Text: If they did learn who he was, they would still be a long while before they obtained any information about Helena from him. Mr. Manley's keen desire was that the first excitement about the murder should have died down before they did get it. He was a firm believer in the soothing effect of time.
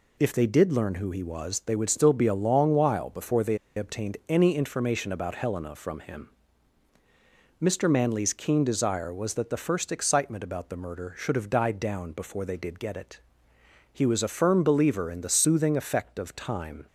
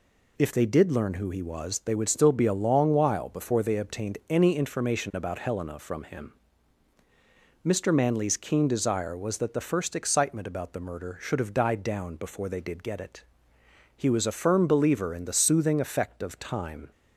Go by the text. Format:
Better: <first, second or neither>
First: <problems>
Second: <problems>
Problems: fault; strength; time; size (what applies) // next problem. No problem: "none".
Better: second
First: pauses between "they" and "obtained"; slight; at 3.5 s; 0.19 s long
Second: none